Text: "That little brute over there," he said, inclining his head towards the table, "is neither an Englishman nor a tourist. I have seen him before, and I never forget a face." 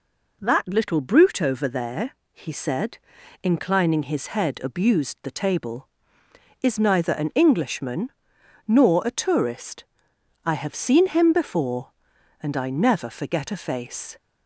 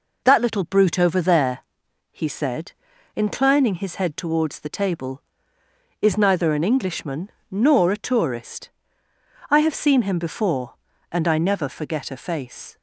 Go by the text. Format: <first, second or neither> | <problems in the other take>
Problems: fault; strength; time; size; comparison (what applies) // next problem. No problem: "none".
second | says "abused" for "towards"; at 4.6 s // pauses between "Englishman" and "nor"; noticeable; at 8.0 s; 0.56 s long; slight in the second